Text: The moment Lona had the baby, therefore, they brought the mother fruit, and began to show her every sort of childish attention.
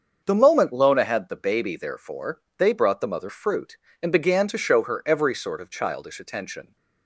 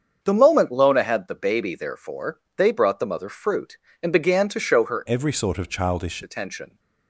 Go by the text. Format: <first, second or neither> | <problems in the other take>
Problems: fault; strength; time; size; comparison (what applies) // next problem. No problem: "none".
first | starts louder than the rest; strong; until 1.2 s; 7 dB; also in the first // changes voice from "every" to "childish"; from 5.0 to 6.2 s; 1.2 s long